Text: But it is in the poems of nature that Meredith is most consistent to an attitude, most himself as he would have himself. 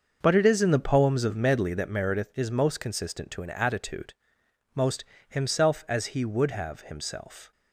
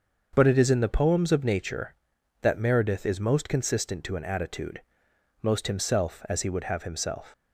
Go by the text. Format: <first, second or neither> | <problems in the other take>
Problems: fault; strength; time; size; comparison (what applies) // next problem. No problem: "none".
second | starts louder than the rest; until 1.2 s; 6.5 dB; also in the second // says "medley" for "nature"; at 1.3 s // pauses between "most" and "himself"; slight; at 5.0 s; 0.24 s long